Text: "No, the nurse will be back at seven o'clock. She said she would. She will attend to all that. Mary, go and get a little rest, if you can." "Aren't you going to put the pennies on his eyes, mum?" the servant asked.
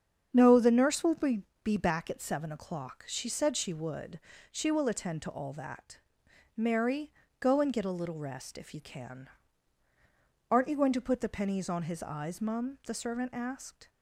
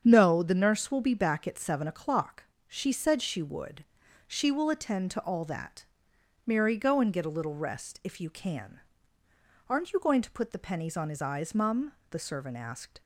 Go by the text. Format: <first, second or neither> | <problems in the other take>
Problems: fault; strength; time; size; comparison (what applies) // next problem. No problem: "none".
second | starts louder than the rest; strong; until 1.3 s; 7.5 dB; strong in the second // says "be" twice; at 1.6 s